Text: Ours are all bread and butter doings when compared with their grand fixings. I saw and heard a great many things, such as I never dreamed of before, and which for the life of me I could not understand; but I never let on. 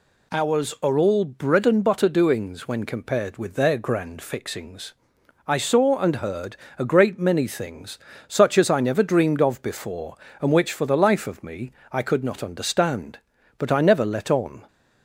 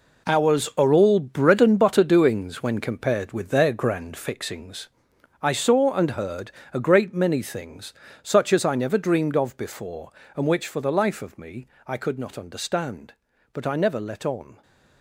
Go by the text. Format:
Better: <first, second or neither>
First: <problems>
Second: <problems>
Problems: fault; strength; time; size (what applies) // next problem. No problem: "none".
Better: first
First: pauses between "heard" and "a"; slight; at 6.5 s; 0.22 s long // pauses between "me" and "I"; slight; at 11.7 s; 0.20 s long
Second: gets quieter; strong; throughout; 11 dB // pauses between "heard" and "a"; slight; at 6.4 s; 0.22 s long // pauses between "me" and "I"; slight; at 11.6 s; 0.20 s long